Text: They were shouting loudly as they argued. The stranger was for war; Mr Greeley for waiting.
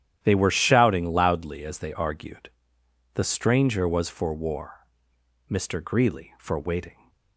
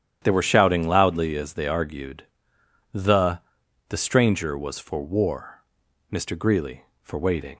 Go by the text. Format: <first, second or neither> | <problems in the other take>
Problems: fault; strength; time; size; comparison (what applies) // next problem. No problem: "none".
first | starts louder than the rest; strong; until 1.2 s; 10 dB; strong in the first // says "The" twice; at 3.8 s